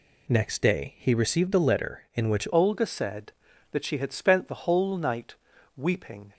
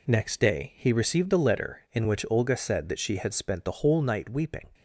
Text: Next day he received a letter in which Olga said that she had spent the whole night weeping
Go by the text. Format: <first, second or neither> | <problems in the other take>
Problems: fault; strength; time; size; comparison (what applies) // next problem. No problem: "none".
second | changes voice at "Olga"; from 2.5 s on; 3.8 s long // pauses between "night" and "weeping"; at 5.3 s; 0.42 s long